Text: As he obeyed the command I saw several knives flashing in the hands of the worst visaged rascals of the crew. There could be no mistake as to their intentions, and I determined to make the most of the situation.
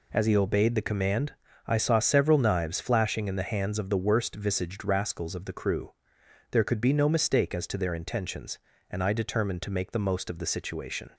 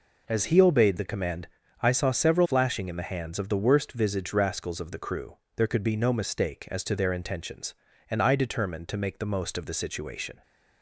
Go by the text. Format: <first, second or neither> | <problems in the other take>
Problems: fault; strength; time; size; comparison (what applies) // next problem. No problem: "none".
first | pauses between "command" and "I"; slight; at 1.4 s; 0.34 s long; slight in the first // skips "knives"; at 2.4 s